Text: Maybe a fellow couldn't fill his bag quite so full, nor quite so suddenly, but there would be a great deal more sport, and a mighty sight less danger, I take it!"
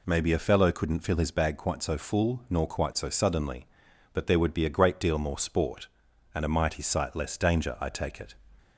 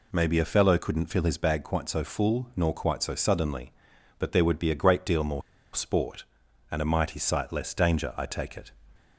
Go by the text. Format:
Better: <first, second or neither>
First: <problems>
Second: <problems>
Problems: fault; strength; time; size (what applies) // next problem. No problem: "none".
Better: first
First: none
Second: pauses between "more" and "sport"; slight; at 5.4 s; 0.34 s long